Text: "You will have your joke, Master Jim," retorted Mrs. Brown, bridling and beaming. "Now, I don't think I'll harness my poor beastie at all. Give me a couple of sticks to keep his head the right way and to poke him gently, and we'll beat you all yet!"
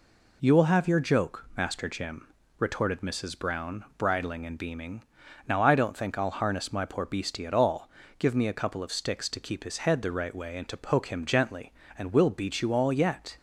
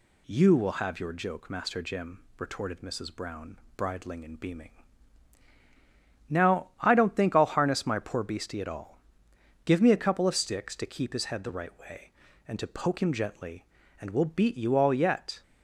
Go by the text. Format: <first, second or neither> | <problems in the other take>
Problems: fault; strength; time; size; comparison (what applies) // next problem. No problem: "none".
neither | none